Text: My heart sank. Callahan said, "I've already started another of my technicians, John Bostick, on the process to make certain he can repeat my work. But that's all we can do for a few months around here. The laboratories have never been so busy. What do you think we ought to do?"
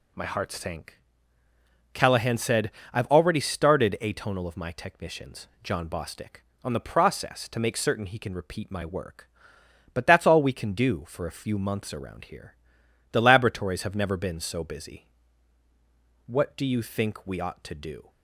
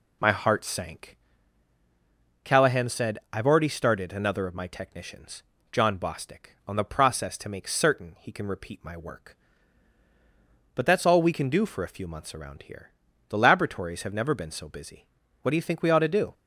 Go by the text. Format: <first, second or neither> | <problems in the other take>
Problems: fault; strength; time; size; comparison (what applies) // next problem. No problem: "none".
second | says "atonal" for "another"; at 3.9 s